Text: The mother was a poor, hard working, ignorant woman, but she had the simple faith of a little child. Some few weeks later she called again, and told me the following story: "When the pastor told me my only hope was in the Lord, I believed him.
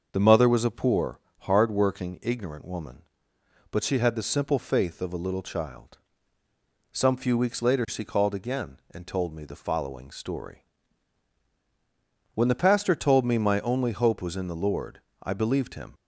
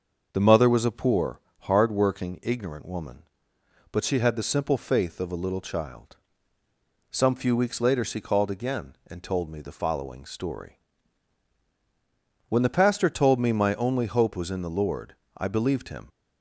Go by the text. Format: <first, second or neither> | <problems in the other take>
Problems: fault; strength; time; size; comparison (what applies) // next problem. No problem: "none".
neither | starts louder than the rest; the same in both